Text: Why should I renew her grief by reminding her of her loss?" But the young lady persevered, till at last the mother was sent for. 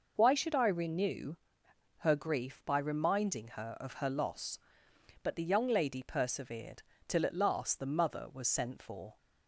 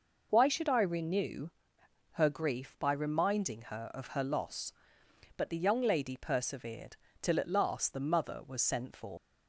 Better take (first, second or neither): first